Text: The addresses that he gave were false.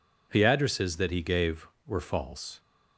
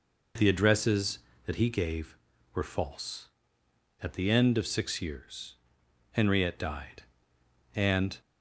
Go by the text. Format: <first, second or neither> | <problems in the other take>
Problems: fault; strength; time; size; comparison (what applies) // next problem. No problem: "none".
first | goes on to say "At the end of six years Henriette died and"; strong; from 4.0 s on; 4.1 s long